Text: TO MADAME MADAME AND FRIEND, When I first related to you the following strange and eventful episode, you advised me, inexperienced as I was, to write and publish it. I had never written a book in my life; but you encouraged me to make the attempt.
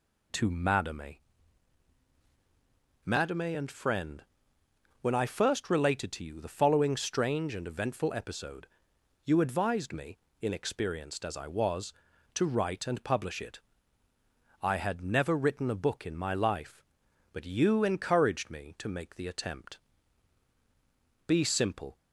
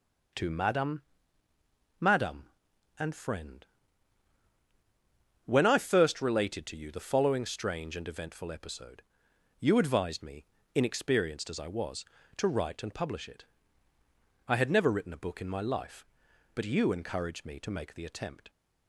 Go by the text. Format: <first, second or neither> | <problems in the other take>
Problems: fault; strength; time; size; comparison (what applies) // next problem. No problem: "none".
second | pauses between "MADAME" and "MADAME"; strong; at 1.1 s; 1.8 s long; noticeable in the second // goes on to say "Be simple"; noticeable; from 21.2 s on; 0.70 s long